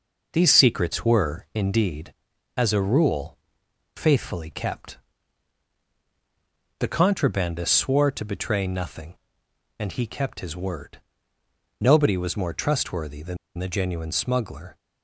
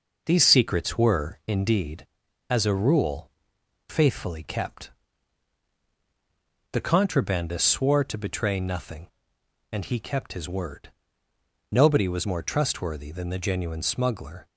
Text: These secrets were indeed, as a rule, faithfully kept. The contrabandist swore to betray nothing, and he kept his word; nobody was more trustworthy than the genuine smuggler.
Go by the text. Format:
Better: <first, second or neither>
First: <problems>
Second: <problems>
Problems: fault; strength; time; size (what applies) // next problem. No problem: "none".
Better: second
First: pauses between "than" and "the"; slight; at 13.3 s; 0.20 s long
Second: none